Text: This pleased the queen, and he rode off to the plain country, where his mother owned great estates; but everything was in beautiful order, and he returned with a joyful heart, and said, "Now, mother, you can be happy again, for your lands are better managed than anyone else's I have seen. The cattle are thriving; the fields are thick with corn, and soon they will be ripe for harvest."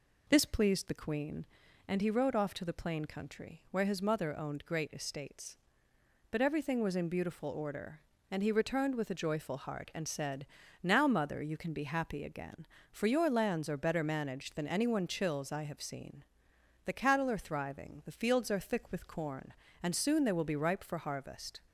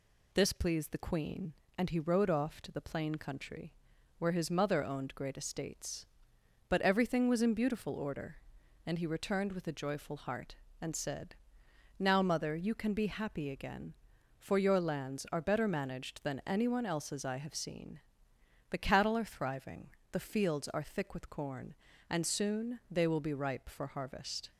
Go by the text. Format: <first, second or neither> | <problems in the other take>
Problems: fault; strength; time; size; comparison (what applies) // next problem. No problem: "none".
second | says "chills" for "else's"; at 15.0 s